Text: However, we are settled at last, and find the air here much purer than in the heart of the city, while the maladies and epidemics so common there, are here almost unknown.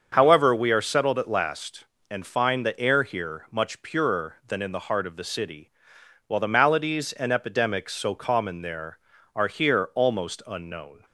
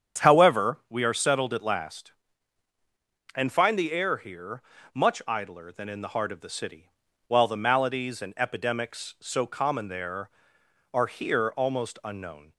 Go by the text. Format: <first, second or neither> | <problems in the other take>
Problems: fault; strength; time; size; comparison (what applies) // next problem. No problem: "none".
first | starts louder than the rest; strong; until 1.2 s; 8 dB; also in the first // pauses between "here" and "much"; slight; at 4.6 s; 0.32 s long // says "idler" for "purer"; at 5.2 s